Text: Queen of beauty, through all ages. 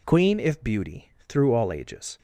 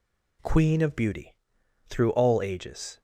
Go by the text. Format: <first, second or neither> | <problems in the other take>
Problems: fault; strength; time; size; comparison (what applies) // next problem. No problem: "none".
second | says "if" for "of"; at 0.3 s